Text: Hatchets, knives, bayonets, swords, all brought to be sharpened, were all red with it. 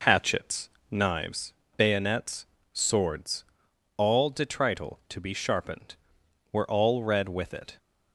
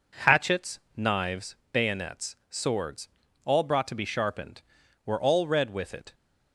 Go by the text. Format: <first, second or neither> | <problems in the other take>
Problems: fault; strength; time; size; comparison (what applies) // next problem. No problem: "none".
second | says "detrital" for "brought"; at 4.3 s